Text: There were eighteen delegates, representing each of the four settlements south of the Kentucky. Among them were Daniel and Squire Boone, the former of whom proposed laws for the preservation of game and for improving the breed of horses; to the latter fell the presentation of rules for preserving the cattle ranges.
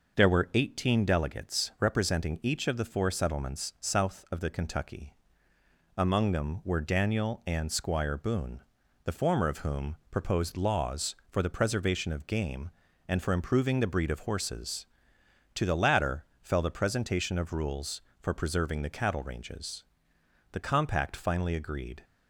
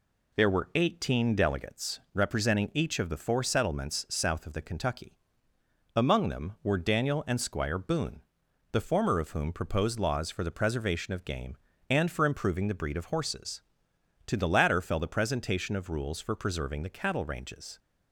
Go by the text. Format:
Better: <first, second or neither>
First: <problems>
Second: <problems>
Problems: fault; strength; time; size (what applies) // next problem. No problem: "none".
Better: second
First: pauses between "whom" and "proposed"; slight; at 9.9 s; 0.16 s long // pauses between "latter" and "fell"; slight; at 16.2 s; 0.18 s long // goes on to say "The compact finally agreed"; from 20.5 s on; 1.5 s long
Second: none